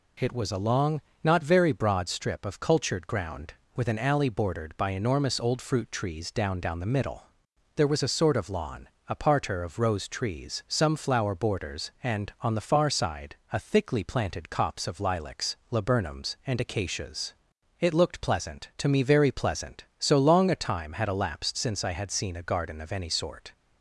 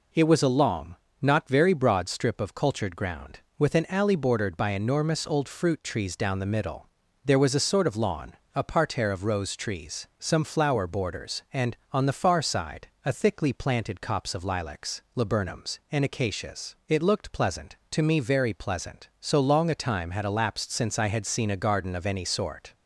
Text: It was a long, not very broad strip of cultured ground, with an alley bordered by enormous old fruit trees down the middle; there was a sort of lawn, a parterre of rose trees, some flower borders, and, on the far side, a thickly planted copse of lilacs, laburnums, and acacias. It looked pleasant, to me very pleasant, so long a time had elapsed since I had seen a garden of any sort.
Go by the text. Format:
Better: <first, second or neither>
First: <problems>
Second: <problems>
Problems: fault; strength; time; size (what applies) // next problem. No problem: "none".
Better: second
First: says "down" twice; at 6.5 s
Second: none